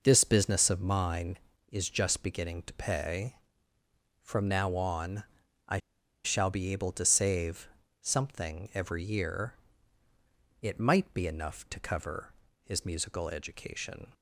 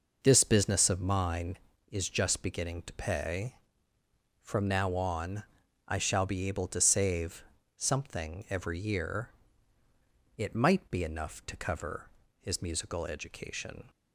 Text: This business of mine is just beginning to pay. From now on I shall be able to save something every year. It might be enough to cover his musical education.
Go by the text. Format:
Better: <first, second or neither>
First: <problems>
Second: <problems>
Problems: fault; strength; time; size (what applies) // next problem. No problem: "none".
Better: second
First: pauses between "on" and "I"; noticeable; at 5.2 s; 0.46 s long // pauses between "I" and "shall"; at 5.7 s; 0.45 s long // pauses between "save" and "something"; slight; at 7.6 s; 0.34 s long // pauses between "cover" and "his"; slight; at 12.3 s; 0.32 s long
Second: pauses between "on" and "I"; noticeable; at 5.4 s; 0.46 s long // pauses between "save" and "something"; slight; at 7.4 s; 0.34 s long // pauses between "cover" and "his"; slight; at 12.0 s; 0.32 s long